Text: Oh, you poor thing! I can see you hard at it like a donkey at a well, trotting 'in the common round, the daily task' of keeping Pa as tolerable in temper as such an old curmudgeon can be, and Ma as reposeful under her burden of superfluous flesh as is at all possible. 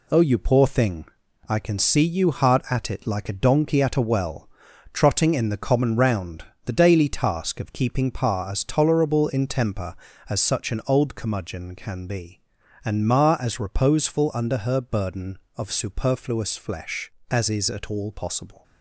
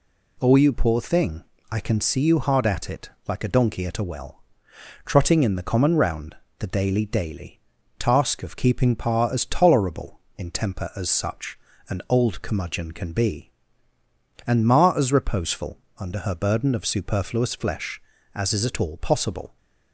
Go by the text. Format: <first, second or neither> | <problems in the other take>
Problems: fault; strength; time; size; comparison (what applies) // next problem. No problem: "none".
first | pauses between "it" and "like"; slight; at 3.0 s; 0.18 s long // says "daily" twice; at 7.0 s // pauses between "such" and "an"; slight; at 11.5 s; 0.30 s long // pauses between "reposeful" and "under"; slight; at 15.7 s; 0.22 s long